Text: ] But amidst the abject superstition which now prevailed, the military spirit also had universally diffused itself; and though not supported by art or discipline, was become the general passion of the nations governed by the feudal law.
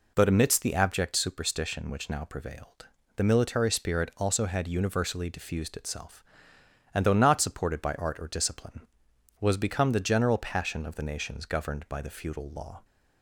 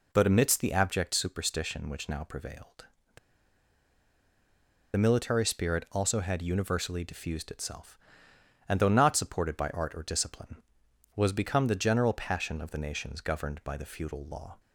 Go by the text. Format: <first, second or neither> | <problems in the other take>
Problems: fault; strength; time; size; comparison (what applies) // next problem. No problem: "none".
first | pauses between "the" and "military"; strong; at 3.1 s; 1.7 s long